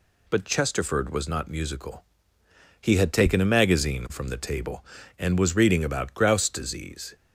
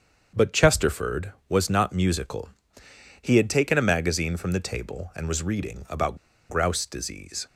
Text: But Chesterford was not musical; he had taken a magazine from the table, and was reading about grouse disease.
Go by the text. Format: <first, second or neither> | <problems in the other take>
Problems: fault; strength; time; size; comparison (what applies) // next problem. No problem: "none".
first | starts louder than the rest; strong; until 1.5 s; 7.5 dB // pauses between "about" and "grouse"; slight; at 6.1 s; 0.32 s long